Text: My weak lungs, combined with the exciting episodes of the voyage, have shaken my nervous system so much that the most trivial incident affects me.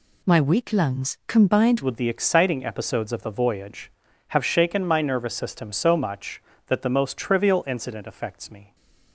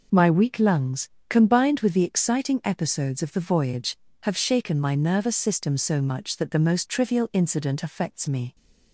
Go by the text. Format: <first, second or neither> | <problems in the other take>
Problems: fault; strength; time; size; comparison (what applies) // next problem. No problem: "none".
second | changes voice at "with"; from 1.8 s on; 6.9 s long